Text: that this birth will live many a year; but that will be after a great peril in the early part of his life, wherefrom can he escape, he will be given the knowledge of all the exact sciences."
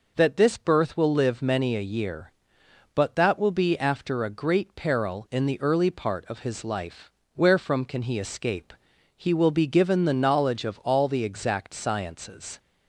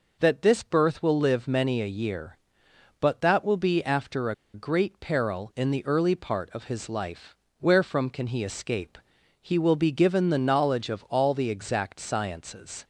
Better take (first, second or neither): first